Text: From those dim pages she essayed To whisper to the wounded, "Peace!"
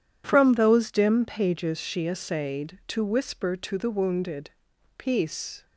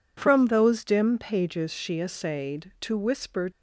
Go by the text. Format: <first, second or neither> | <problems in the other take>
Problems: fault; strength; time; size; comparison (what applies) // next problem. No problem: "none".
first | stops before "to the wounded Peace"; at 3.5 s